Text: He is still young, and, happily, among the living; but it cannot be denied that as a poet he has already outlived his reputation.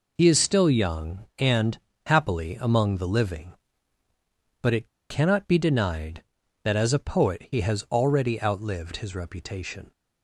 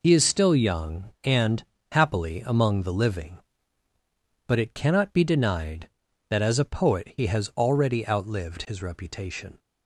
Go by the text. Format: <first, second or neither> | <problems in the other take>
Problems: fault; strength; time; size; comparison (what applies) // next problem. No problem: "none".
second | pauses between "it" and "cannot"; slight; at 4.8 s; 0.21 s long